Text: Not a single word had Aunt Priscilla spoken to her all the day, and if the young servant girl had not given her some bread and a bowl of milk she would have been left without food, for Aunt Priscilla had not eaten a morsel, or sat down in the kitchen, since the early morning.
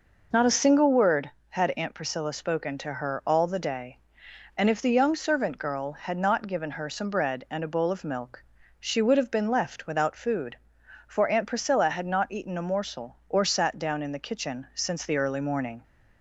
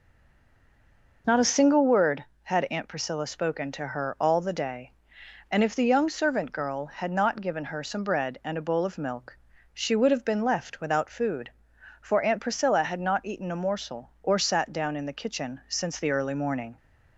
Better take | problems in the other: first | stays silent before the first word; noticeable; until 1.2 s; 1.2 s long // pauses between "milk" and "she"; at 9.3 s; 0.38 s long; also in the first

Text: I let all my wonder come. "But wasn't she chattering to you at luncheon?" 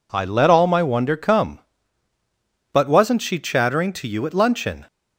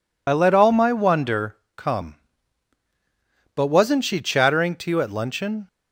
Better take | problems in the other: first | loses the start of "I"; at 0.2 s; 40 ms // pauses between "wonder" and "come"; slight; at 1.5 s; 0.18 s long

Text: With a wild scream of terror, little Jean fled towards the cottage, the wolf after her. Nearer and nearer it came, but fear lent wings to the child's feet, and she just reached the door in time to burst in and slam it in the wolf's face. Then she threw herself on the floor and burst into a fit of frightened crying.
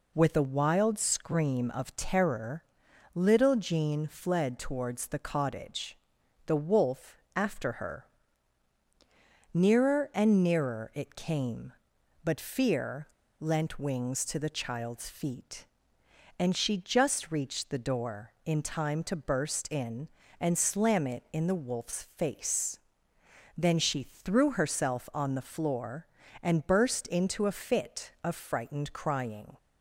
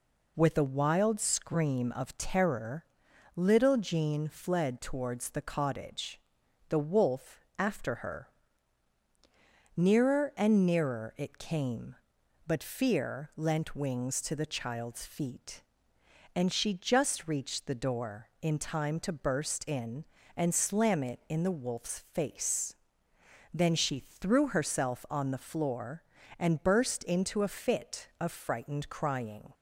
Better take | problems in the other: second | pauses between "wolf" and "after"; slight; at 7.1 s; 0.18 s long; slight in the second // pauses between "fear" and "lent"; slight; at 13.0 s; 0.32 s long

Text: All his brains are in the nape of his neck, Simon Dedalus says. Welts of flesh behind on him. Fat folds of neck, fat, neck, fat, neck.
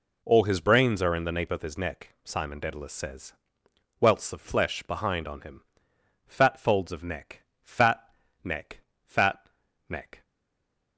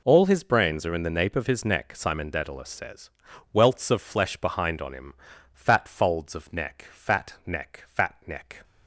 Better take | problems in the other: second | stays silent after the last word; slight; from 10.2 s on; 0.7 s long

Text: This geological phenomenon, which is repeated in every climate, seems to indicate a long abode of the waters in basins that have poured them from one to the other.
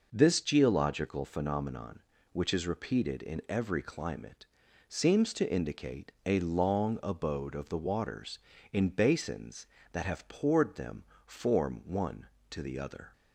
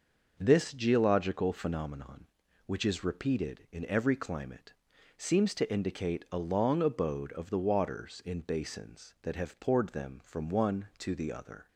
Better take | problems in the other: second | says "form" for "from"; at 11.2 s

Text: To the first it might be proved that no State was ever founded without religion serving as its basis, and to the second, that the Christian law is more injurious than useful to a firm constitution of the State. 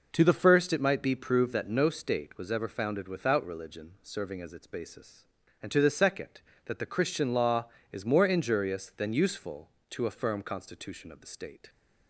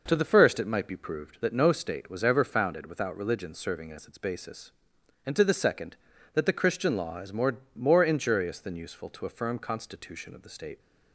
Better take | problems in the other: first | says "more" twice; at 7.7 s

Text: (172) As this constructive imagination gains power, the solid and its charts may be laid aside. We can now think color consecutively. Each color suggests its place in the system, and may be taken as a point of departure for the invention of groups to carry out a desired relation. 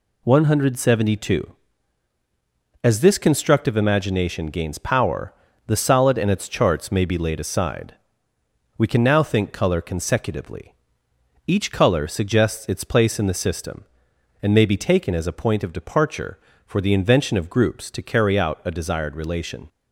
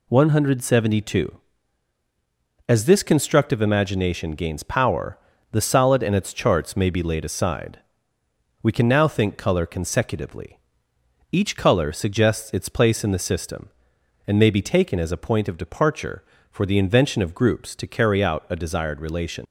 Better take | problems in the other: first | leaves "relation" unfinished; at 19.4 s; 75 ms

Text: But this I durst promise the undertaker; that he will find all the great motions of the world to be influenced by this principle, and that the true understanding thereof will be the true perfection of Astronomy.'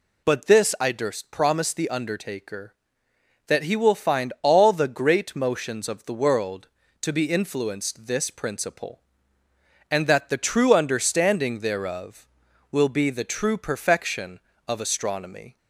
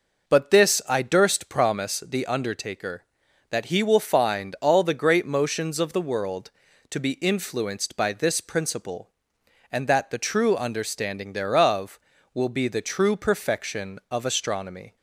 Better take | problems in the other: second | skips "by"; at 8.0 s

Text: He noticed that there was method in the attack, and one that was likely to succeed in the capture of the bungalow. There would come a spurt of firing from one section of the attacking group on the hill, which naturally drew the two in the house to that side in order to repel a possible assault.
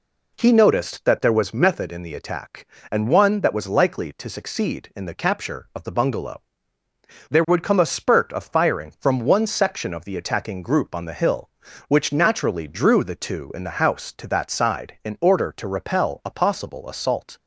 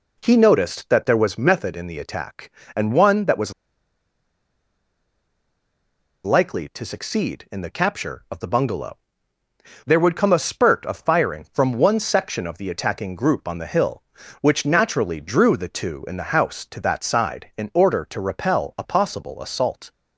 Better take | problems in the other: first | pauses between "was" and "likely"; strong; at 3.5 s; 2.7 s long

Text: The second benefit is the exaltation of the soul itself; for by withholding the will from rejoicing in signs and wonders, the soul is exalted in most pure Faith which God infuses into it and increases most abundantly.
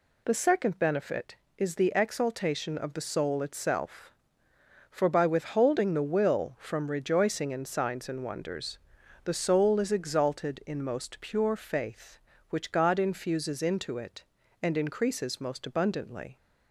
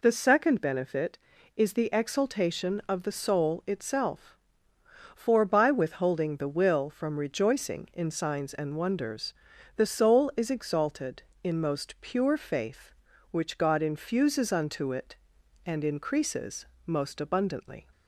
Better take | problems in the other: first | says "unto" for "into"; at 14.5 s // pauses between "increases" and "most"; slight; at 16.6 s; 0.18 s long

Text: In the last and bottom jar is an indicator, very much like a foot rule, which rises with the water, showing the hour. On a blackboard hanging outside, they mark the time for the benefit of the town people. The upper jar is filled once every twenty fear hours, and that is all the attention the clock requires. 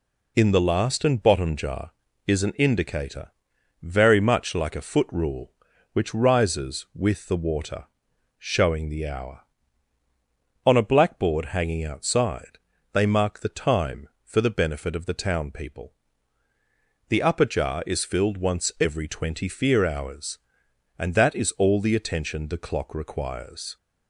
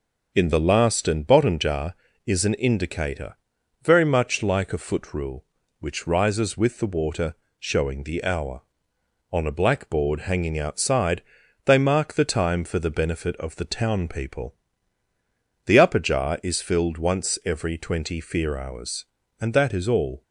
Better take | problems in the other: first | stops before "the attention the clock requires"; at 20.2 s

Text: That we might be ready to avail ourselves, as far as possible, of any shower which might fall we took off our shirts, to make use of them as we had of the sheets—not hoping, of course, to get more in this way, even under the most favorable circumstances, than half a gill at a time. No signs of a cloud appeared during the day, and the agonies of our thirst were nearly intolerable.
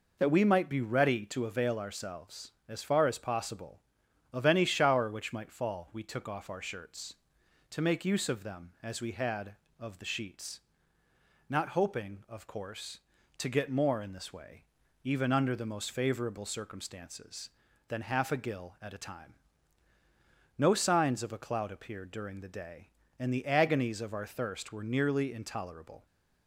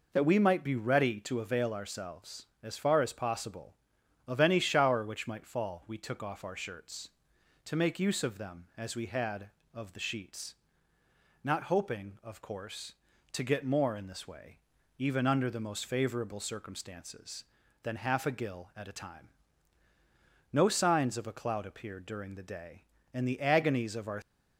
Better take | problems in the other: first | stops before "thirst were nearly intolerable"; at 24.2 s

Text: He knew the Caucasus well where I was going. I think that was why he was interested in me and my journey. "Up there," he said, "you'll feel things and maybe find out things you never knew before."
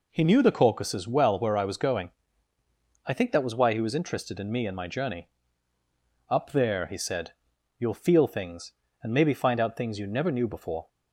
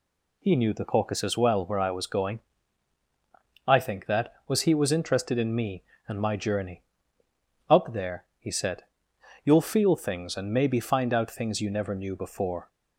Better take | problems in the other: first | skips "why"; at 4.6 s

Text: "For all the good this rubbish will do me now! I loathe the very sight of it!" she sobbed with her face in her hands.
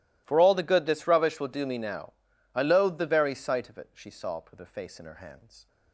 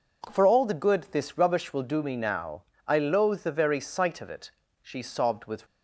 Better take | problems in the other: first | stops before "her face in her hands"; at 5.6 s

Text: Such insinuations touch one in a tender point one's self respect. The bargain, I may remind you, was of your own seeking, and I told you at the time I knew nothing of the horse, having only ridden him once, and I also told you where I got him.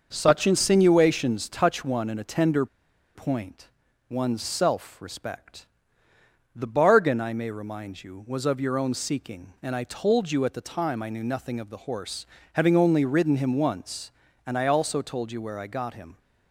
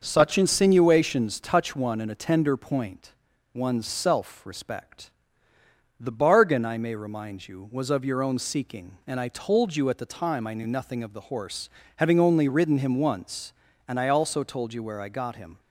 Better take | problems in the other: second | starts louder than the rest; until 1.1 s; 6.5 dB; also in the second // pauses between "tender" and "point"; noticeable; at 2.6 s; 0.49 s long // pauses between "point" and "one's"; at 3.6 s; 0.42 s long; also in the second

